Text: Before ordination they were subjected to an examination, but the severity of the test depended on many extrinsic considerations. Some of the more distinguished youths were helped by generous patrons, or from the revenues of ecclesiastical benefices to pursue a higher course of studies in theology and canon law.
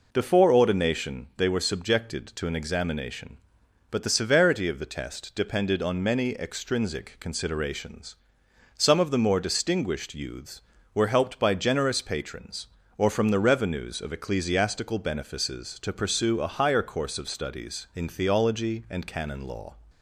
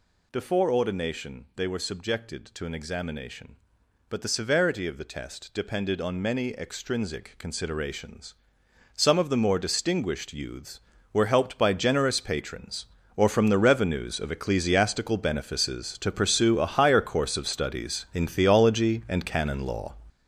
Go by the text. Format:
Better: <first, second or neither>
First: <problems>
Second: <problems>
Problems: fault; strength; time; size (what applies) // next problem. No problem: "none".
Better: first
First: none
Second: gets louder; strong; throughout; 8 dB